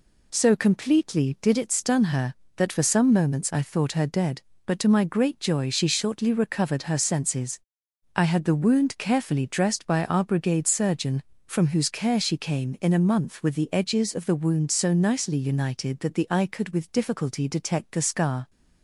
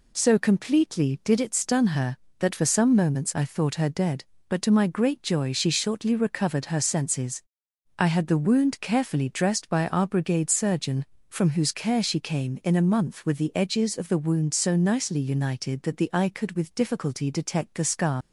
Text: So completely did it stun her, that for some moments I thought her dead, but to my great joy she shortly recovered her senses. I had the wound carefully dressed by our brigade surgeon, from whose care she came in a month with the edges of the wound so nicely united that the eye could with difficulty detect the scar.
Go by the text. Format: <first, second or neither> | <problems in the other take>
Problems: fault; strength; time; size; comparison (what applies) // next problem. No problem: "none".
first | leaves "scar" unfinished; at 18.2 s; 115 ms